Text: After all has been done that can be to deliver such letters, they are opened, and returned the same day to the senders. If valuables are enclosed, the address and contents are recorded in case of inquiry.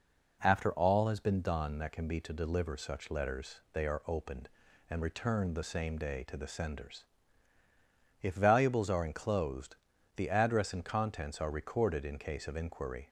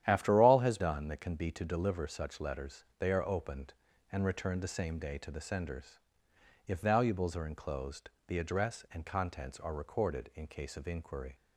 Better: first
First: none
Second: starts louder than the rest; strong; until 1.0 s; 10.5 dB // skips "been"; at 0.7 s

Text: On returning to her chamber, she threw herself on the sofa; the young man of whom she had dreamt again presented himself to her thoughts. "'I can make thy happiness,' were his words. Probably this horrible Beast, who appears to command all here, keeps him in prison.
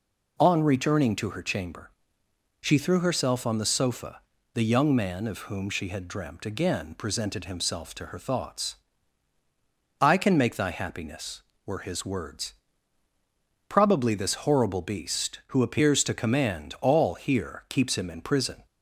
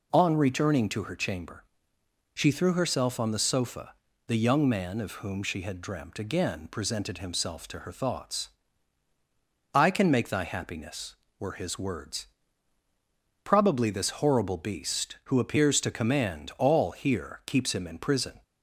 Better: neither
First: none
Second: none

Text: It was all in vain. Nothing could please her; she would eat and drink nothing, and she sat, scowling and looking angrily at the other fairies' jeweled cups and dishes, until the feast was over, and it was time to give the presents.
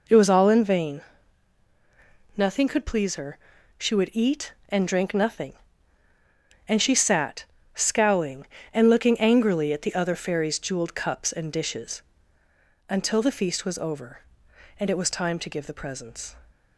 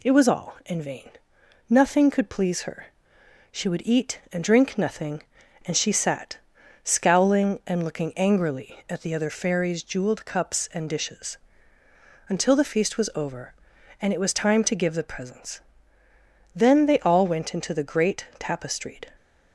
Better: first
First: none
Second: goes on to say "Then they all went into the great tapestried"; strong; from 16.5 s on; 2.5 s long

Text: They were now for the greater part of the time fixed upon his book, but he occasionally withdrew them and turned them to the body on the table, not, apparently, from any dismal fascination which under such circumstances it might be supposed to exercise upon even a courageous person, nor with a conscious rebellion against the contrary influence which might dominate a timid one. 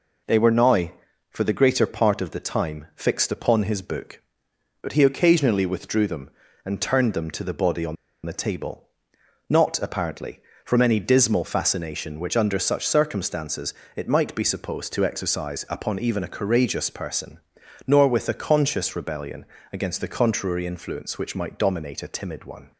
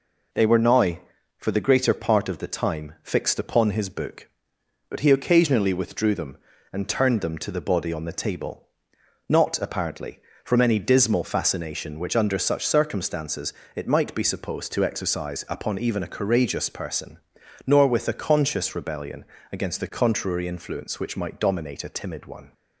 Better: second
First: pauses between "on" and "the"; slight; at 7.9 s; 0.30 s long // pauses between "circumstances" and "it"; slight; at 13.7 s; 0.22 s long // pauses between "rebellion" and "against"; slight; at 19.4 s; 0.26 s long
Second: pauses between "circumstances" and "it"; slight; at 13.5 s; 0.22 s long // pauses between "rebellion" and "against"; slight; at 19.2 s; 0.26 s long

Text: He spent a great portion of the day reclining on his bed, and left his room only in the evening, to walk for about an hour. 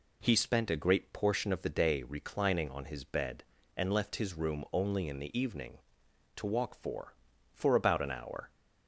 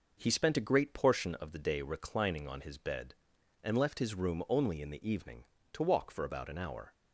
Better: second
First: says "for" twice; at 7.5 s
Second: none

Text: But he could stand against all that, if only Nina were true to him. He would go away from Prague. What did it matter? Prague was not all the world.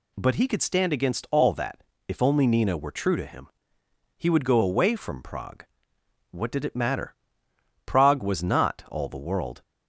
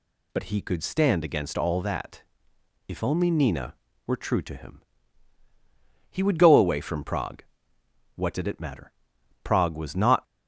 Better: first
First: none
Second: stops before "all the world"; at 10.2 s

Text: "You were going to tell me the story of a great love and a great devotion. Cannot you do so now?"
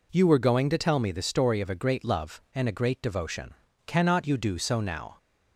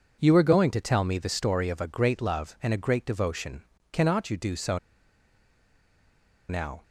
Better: first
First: none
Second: pauses between "so" and "now"; strong; at 4.7 s; 1.7 s long

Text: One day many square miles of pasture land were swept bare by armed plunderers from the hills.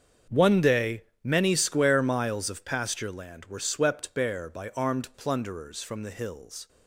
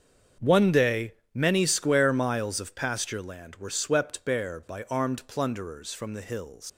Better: first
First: starts louder than the rest; strong; until 1.4 s; 7 dB // pauses between "day" and "many"; slight; at 1.0 s; 0.18 s long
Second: starts louder than the rest; strong; until 1.6 s; 7 dB // pauses between "day" and "many"; slight; at 1.1 s; 0.18 s long // leaves "hills" unfinished; at 6.6 s; 85 ms

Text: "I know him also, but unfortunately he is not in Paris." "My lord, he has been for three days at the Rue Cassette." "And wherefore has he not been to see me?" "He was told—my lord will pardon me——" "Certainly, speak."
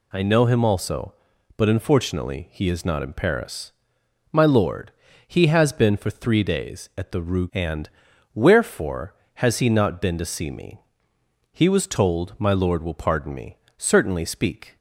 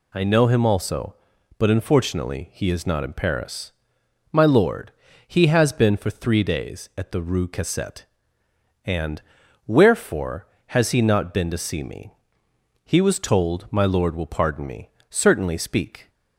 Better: second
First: skips "Cassette"; at 7.4 s // pauses between "And" and "wherefore"; noticeable; at 7.8 s; 0.46 s long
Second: pauses between "And" and "wherefore"; noticeable; at 9.2 s; 0.46 s long

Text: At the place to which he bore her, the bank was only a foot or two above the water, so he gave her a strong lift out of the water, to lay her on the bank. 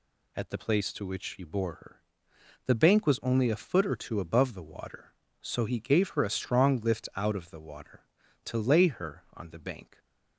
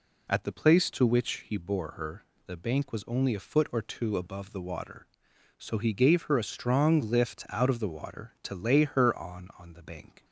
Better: first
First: none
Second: says "on" twice; at 9.5 s

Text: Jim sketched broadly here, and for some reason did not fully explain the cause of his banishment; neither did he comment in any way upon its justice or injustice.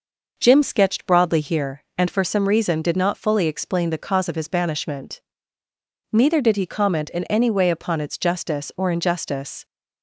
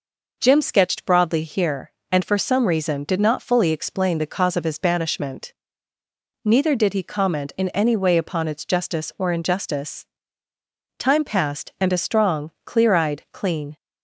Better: first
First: none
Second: goes on to say "Time passed and a strong clear eyed clean"; strong; from 10.9 s on; 2.7 s long

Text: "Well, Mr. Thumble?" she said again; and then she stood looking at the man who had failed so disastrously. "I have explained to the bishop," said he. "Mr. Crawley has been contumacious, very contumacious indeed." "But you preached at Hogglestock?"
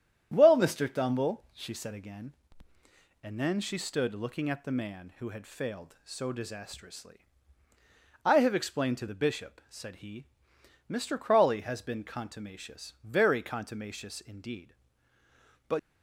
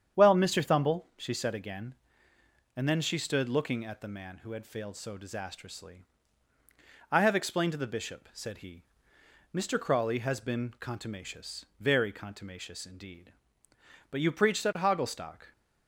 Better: second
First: starts louder than the rest; strong; until 1.3 s; 9.5 dB // stops before "you preached at Hogglestock"; at 15.7 s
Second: starts louder than the rest; strong; until 1.2 s; 8.5 dB

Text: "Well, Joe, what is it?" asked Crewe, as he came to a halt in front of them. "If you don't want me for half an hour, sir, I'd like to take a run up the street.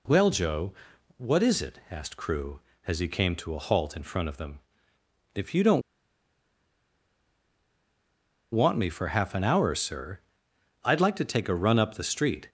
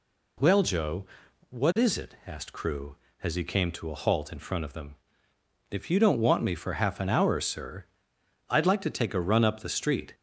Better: second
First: pauses between "don't" and "want"; strong; at 5.8 s; 2.7 s long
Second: none

